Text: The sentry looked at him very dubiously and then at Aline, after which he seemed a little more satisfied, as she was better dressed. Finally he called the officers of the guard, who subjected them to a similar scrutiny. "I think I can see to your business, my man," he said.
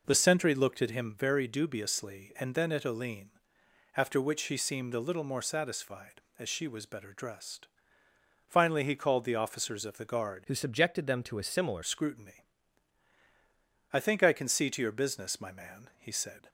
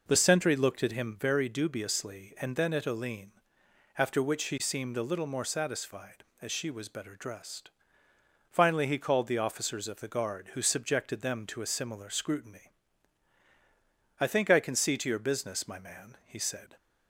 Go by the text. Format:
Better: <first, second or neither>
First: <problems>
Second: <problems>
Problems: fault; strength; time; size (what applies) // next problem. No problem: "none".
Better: second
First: changes voice from "who" to "similar"; from 10.4 to 11.8 s; 1.4 s long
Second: none